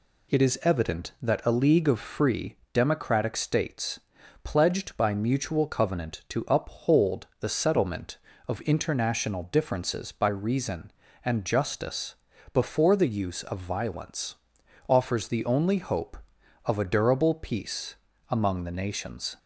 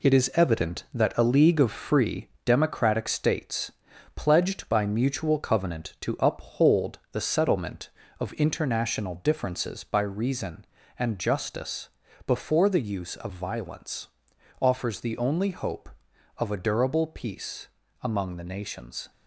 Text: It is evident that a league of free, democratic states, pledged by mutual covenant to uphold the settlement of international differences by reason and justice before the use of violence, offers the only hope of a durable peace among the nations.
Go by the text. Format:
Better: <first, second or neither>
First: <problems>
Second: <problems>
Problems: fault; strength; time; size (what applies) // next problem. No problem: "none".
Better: first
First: pauses between "justice" and "before"; slight; at 12.1 s; 0.36 s long // pauses between "peace" and "among"; slight; at 17.9 s; 0.34 s long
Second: gets quieter; noticeable; throughout; 6 dB // pauses between "justice" and "before"; slight; at 11.8 s; 0.35 s long // pauses between "peace" and "among"; slight; at 17.6 s; 0.34 s long